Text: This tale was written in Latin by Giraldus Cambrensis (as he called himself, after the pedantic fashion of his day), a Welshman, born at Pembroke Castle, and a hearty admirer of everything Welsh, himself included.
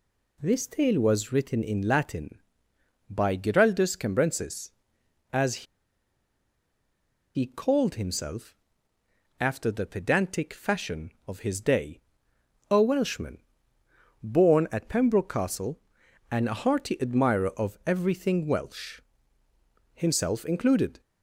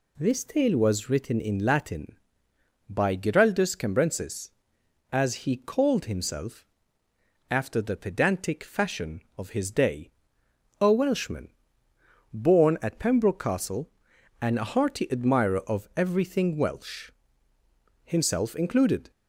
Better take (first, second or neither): second